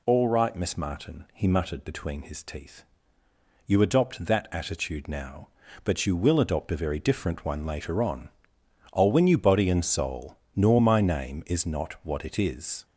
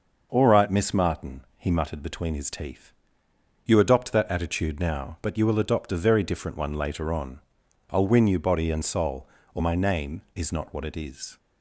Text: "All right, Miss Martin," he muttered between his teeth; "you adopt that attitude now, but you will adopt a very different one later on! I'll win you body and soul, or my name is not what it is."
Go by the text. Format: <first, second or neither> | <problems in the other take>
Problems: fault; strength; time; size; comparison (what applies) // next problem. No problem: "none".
second | says "nor" for "or"; at 10.5 s